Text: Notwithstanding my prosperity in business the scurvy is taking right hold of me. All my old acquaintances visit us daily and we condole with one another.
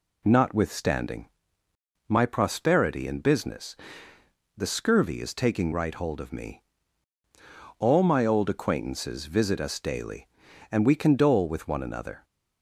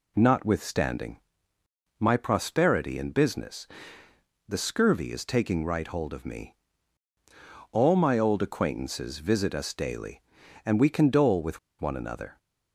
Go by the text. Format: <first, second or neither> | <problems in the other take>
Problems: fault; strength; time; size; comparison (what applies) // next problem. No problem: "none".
first | pauses between "Notwithstanding" and "my"; noticeable; at 1.1 s; 0.80 s long; noticeable in the first // pauses between "business" and "the"; noticeable; at 3.6 s; 0.82 s long; noticeable in the first // pauses between "with" and "one"; slight; at 11.5 s; 0.22 s long